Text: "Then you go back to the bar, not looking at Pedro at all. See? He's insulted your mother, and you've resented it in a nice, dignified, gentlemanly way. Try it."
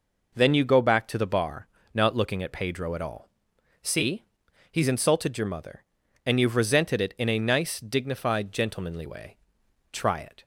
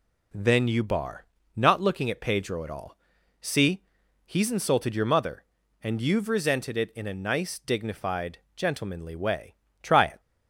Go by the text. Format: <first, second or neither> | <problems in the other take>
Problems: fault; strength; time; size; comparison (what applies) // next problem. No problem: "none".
first | skips "go back to the"; at 0.8 s